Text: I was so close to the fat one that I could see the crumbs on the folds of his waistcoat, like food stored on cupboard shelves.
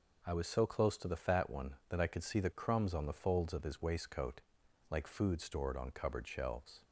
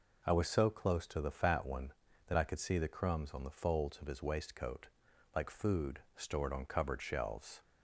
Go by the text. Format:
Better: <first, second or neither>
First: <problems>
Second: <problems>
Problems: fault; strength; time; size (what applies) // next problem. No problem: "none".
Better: neither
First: none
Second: none